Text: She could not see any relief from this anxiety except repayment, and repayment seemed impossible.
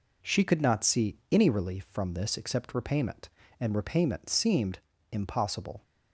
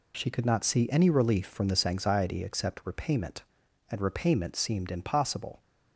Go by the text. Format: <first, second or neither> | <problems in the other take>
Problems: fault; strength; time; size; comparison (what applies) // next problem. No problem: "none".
second | skips "anxiety"; at 2.3 s // pauses between "seemed" and "impossible"; slight; at 4.7 s; 0.32 s long